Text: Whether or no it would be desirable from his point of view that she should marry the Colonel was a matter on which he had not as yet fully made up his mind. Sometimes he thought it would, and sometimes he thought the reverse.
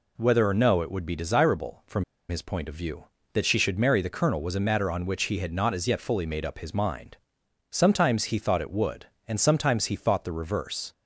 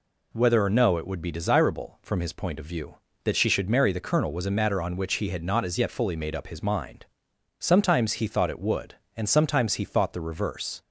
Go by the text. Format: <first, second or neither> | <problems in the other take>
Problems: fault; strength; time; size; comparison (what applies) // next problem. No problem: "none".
second | pauses between "from" and "his"; slight; at 2.0 s; 0.26 s long